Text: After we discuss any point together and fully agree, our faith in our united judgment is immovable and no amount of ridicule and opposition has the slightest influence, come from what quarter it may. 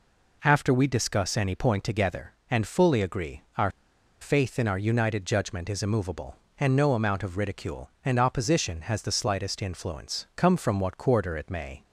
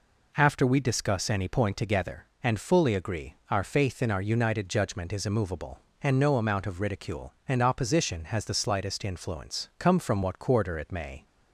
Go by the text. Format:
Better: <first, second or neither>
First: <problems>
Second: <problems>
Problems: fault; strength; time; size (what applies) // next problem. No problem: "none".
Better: second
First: pauses between "our" and "faith"; noticeable; at 3.6 s; 0.51 s long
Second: none